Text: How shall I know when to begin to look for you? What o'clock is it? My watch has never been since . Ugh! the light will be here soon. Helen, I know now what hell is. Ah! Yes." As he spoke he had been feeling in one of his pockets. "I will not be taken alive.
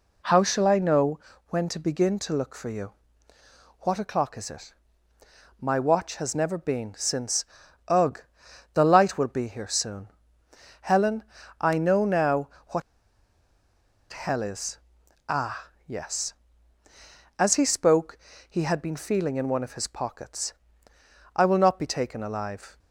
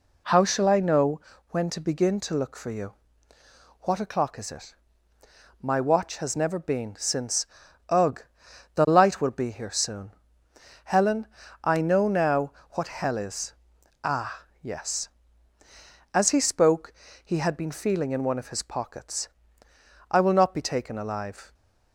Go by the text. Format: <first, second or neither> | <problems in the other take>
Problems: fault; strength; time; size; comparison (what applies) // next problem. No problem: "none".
second | pauses between "know" and "when"; slight; at 1.1 s; 0.30 s long; slight in the second // pauses between "now" and "what"; slight; at 12.4 s; 0.20 s long; slight in the second // pauses between "what" and "hell"; strong; at 12.8 s; 1.3 s long // pauses between "spoke" and "he"; slight; at 18.1 s; 0.32 s long; slight in the second